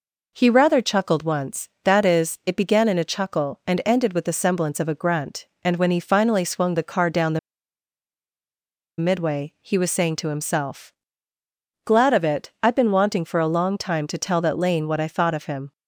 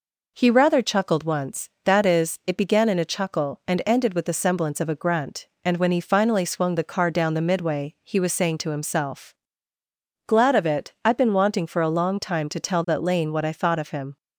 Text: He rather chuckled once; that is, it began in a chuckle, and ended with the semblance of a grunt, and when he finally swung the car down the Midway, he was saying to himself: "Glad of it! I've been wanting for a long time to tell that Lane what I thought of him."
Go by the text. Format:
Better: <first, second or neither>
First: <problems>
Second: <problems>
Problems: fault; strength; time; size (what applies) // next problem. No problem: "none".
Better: second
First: pauses between "the" and "Midway"; strong; at 7.3 s; 1.6 s long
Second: none